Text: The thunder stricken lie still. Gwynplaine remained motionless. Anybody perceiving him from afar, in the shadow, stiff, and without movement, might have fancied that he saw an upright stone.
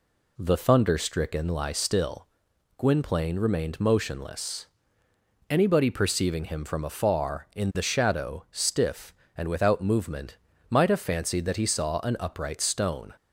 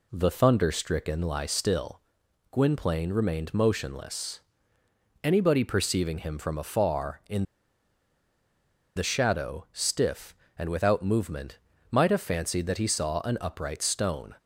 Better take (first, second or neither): first